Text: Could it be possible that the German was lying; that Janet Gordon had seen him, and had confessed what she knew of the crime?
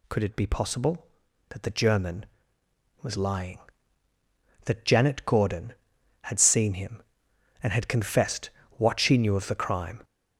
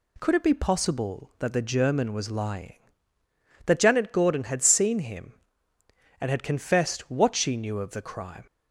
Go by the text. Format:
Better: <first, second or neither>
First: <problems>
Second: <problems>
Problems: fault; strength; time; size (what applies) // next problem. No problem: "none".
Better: second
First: gets louder; throughout; 7 dB // pauses between "confessed" and "what"; slight; at 8.5 s; 0.26 s long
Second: none